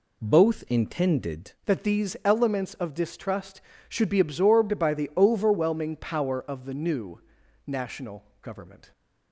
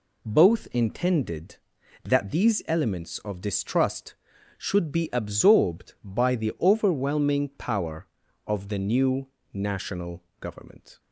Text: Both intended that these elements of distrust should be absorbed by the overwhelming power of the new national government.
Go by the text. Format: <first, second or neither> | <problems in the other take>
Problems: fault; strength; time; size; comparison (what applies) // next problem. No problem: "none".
second | changes voice at "that"; from 1.6 s on; 7.3 s long // pauses between "new" and "national"; noticeable; at 7.1 s; 0.46 s long; slight in the second // pauses between "national" and "government"; slight; at 8.2 s; 0.18 s long; slight in the second